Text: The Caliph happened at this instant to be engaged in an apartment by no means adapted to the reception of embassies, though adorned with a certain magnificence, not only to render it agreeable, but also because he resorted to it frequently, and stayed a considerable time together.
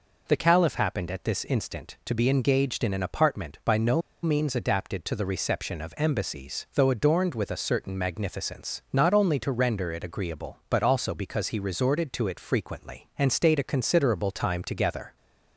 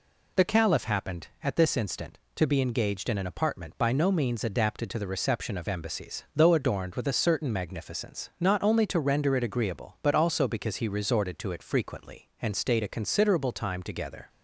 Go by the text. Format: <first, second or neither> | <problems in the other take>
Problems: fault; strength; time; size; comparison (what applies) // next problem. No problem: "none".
second | pauses between "no" and "means"; slight; at 3.9 s; 0.23 s long